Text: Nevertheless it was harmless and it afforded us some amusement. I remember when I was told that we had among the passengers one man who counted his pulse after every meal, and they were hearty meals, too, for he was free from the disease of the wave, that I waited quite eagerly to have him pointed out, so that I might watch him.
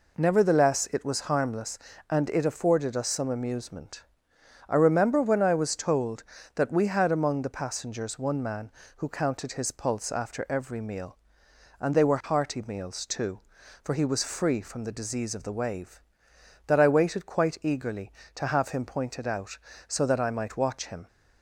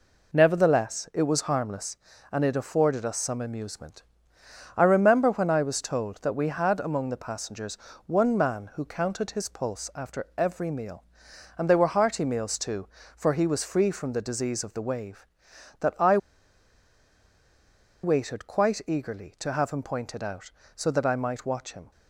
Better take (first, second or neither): first